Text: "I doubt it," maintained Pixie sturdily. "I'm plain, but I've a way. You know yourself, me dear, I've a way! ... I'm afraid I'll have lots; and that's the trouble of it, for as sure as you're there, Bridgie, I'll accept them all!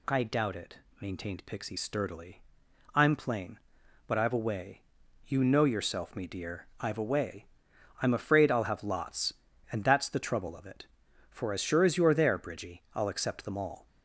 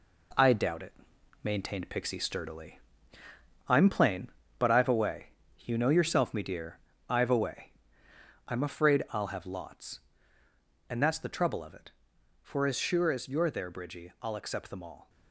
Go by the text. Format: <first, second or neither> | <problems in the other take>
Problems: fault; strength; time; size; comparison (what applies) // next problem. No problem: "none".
first | gets quieter; noticeable; throughout; 6 dB